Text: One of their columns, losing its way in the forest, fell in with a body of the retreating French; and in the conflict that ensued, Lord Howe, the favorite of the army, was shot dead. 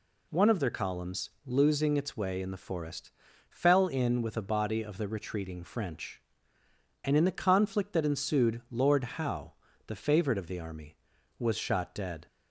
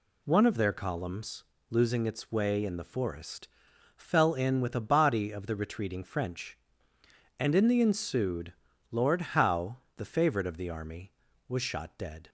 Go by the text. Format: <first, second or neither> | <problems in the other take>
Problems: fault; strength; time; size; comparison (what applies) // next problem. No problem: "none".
first | skips "conflict that"; at 7.8 s